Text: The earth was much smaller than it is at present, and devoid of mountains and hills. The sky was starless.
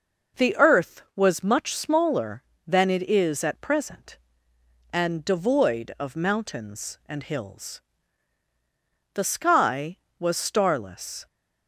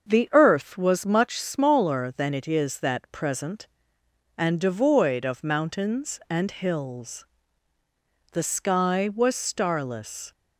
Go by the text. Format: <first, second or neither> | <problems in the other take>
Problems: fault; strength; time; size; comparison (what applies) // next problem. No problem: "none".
first | starts louder than the rest; until 1.1 s; 6.5 dB // says "that" for "at"; at 2.7 s